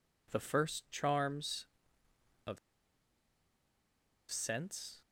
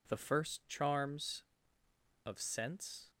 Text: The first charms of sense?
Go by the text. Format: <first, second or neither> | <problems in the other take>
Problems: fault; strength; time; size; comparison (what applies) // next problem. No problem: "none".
second | pauses between "of" and "sense"; strong; at 2.5 s; 1.7 s long